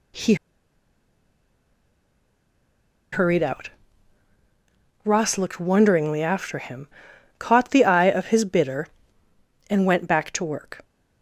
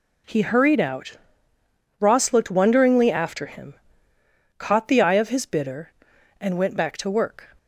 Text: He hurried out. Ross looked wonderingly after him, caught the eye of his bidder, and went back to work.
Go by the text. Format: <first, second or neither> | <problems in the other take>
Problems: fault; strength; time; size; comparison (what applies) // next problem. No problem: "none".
second | pauses between "He" and "hurried"; strong; at 0.3 s; 2.7 s long